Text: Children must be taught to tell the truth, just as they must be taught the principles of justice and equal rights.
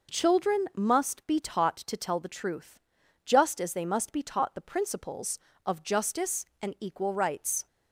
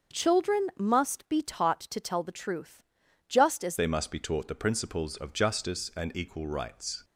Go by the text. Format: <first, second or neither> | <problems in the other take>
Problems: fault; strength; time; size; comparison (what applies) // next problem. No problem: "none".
first | starts louder than the rest; until 1.2 s; 6.5 dB // changes voice at "they"; from 3.7 s on; 3.3 s long